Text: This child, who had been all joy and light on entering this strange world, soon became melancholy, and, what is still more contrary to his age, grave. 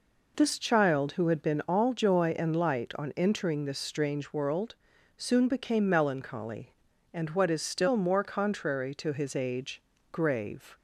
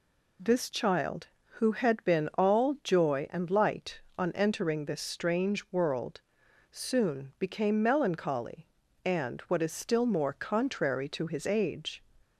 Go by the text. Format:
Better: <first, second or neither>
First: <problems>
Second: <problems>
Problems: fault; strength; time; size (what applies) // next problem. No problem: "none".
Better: first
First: none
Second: stops before "grave"; at 12.2 s